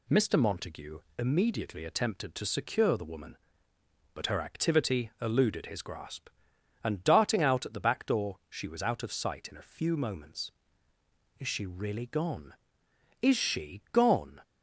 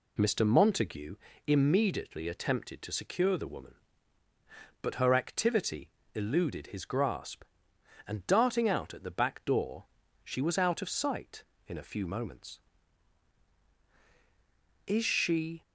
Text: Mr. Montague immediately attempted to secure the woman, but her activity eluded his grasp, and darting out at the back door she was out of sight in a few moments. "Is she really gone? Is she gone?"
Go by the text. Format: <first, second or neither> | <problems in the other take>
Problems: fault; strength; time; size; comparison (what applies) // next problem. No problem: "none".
first | pauses between "Montague" and "immediately"; slight; at 1.1 s; 0.30 s long; slight in the first // pauses between "activity" and "eluded"; slight; at 5.8 s; 0.26 s long // pauses between "door" and "she"; at 9.8 s; 0.38 s long // stops before "really gone Is she gone"; at 15.6 s